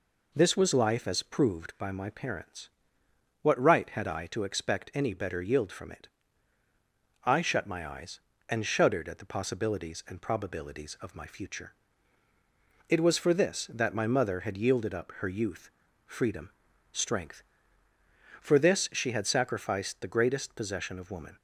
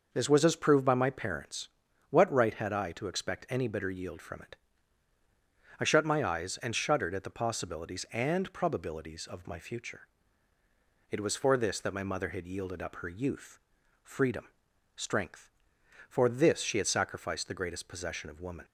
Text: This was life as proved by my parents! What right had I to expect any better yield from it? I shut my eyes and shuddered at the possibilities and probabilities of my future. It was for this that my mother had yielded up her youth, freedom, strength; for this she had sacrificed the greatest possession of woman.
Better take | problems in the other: first | skips "life"; at 0.4 s

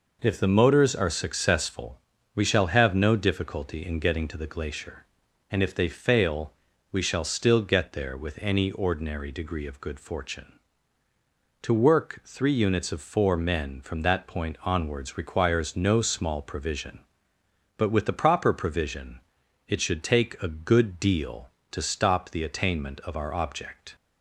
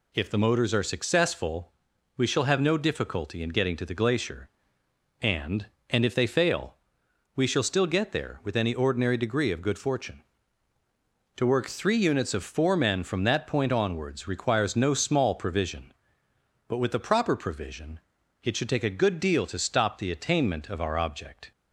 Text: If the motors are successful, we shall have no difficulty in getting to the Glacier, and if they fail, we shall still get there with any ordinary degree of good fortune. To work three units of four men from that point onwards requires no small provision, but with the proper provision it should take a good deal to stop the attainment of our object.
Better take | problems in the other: first | says "and" twice; at 5.8 s // pauses between "provision" and "it"; at 17.9 s; 0.44 s long; noticeable in the first

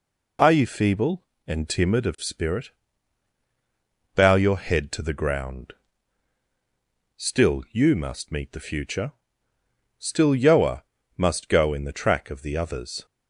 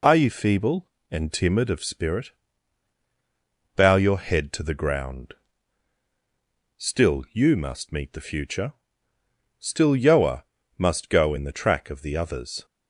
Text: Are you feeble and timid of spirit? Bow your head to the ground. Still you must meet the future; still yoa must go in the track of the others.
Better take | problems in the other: neither | pauses between "yoa" and "must"; slight; the same in both

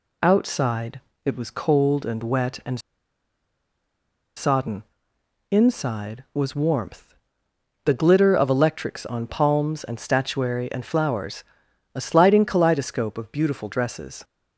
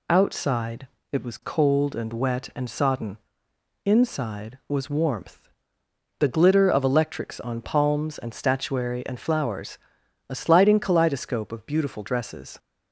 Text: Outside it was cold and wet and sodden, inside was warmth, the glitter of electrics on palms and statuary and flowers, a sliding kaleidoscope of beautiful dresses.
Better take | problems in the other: second | pauses between "Outside" and "it"; slight; at 1.0 s; 0.24 s long; slight in the second // pauses between "and" and "sodden"; strong; at 2.8 s; 1.5 s long

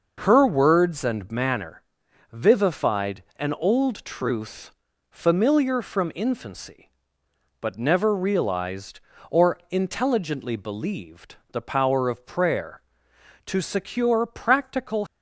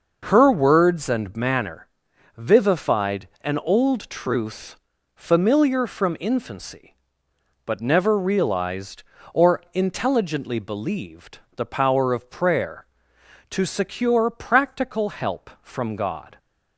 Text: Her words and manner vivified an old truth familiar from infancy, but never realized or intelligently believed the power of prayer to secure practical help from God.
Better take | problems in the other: second | starts louder than the rest; noticeable; until 1.2 s; 6 dB // pauses between "manner" and "vivified"; noticeable; at 1.8 s; 0.52 s long; noticeable in the second // pauses between "truth" and "familiar"; at 4.7 s; 0.40 s long; also in the second // pauses between "believed" and "the"; slight; at 11.3 s; 0.16 s long; slight in the second // stops before "help from God"; at 15.0 s

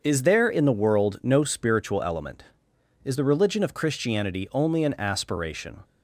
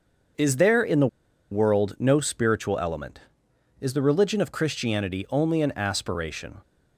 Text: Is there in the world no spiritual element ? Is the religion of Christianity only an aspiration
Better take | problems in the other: first | starts louder than the rest; until 1.8 s; 6.5 dB; also in the first // pauses between "the" and "world"; at 1.0 s; 0.44 s long

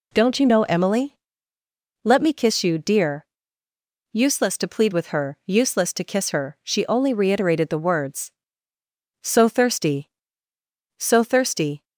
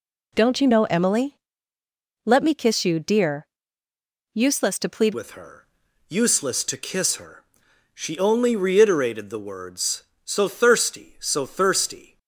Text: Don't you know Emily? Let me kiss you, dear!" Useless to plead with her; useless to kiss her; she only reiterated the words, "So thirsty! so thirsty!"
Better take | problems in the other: first | changes voice at "with"; from 5.1 s on; 7.0 s long

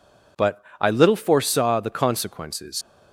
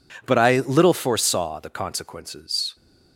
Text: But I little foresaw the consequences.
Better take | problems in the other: second | pauses between "But" and "I"; slight; at 0.6 s; 0.18 s long // leaves "consequences" unfinished; at 2.8 s; 75 ms

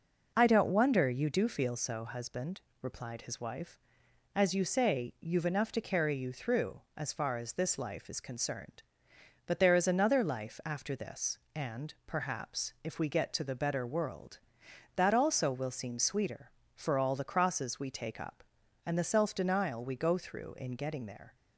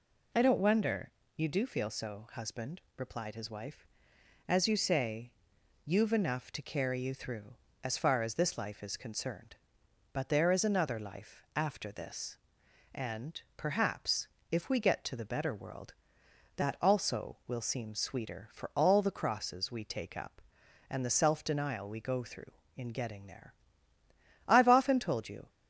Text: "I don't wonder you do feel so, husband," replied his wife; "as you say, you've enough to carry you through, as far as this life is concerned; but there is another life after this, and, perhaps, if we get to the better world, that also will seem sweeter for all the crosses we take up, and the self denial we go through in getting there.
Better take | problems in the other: first | pauses between "wonder" and "you"; slight; at 1.1 s; 0.24 s long // goes on to say "I've often told you"; noticeable; from 24.4 s on; 1.0 s long

